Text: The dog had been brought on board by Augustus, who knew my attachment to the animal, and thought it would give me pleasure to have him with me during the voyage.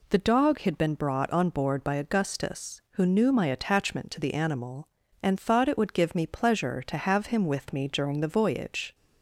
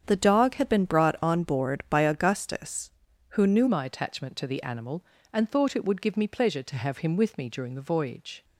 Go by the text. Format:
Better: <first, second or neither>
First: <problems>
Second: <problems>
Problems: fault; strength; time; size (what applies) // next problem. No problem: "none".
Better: first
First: none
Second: starts louder than the rest; strong; until 1.0 s; 8 dB // changes voice at "my"; from 3.6 s on; 4.8 s long